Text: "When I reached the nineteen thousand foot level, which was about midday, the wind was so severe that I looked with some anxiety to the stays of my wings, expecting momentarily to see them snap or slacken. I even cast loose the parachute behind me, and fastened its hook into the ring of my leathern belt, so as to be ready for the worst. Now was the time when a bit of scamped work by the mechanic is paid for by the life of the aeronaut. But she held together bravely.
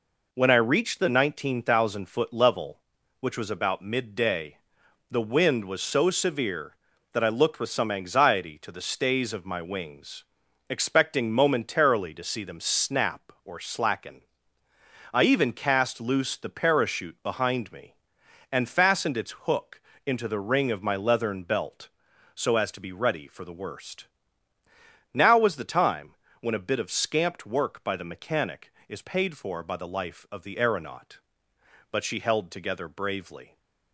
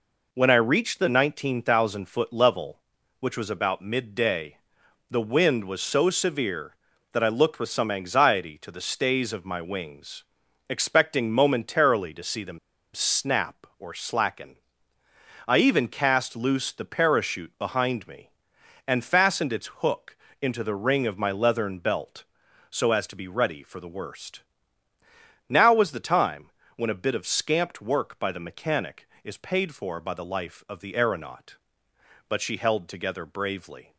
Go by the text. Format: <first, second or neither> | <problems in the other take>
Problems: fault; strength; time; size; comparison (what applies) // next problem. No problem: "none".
first | pauses between "them" and "snap"; at 12.5 s; 0.36 s long // pauses between "hook" and "into"; slight; at 20.1 s; 0.26 s long; slight in the first // pauses between "time" and "when"; slight; at 26.4 s; 0.26 s long; slight in the first